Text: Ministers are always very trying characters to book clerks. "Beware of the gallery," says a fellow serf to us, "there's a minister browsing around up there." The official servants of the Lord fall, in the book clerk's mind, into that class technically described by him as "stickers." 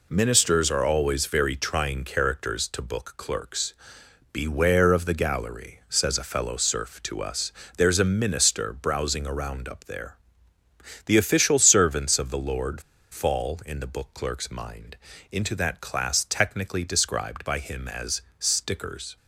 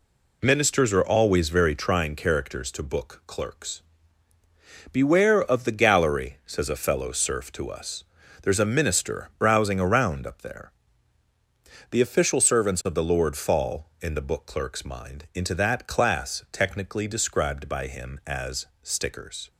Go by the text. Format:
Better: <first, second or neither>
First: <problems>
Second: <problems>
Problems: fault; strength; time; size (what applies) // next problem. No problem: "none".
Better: second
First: pauses between "Lord" and "fall"; slight; at 12.8 s; 0.30 s long // pauses between "as" and "stickers"; slight; at 18.2 s; 0.16 s long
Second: pauses between "as" and "stickers"; slight; at 18.6 s; 0.18 s long